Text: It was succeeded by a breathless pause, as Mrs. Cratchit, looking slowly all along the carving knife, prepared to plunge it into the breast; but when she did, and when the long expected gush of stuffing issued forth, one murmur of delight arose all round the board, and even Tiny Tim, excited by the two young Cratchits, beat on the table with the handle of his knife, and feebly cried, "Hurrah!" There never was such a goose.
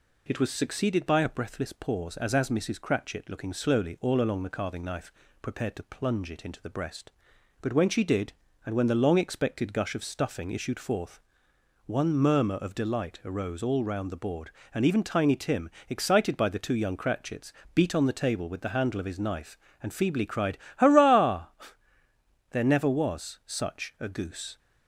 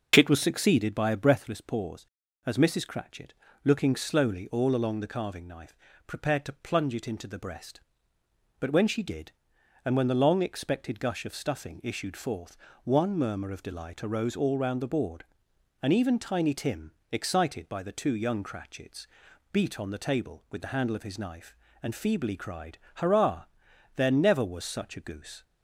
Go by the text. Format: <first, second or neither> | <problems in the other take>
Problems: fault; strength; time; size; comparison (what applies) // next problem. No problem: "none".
second | says "as" twice; at 2.3 s